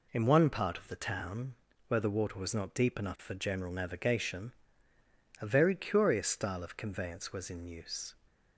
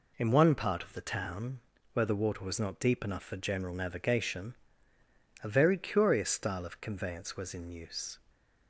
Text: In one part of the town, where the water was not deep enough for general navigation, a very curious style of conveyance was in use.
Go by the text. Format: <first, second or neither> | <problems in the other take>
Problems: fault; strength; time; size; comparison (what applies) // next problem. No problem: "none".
neither | none